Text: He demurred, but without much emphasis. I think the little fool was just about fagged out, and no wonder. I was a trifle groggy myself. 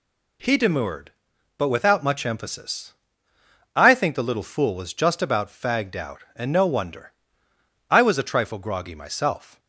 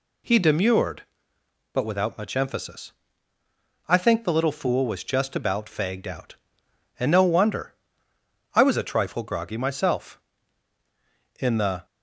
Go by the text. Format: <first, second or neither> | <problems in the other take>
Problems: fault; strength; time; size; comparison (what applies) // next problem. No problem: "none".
first | goes on to say "In the"; slight; from 11.3 s on; 0.46 s long